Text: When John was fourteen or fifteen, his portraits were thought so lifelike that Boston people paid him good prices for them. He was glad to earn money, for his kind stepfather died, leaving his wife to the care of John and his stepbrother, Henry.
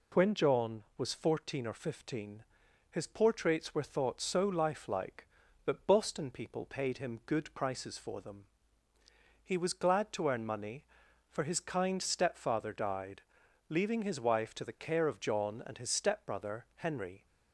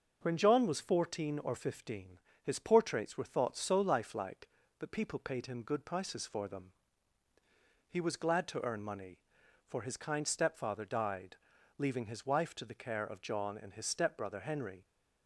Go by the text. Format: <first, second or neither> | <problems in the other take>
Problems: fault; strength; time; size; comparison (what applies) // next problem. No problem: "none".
first | starts louder than the rest; until 1.2 s; 6.5 dB // skips "Boston"; at 4.9 s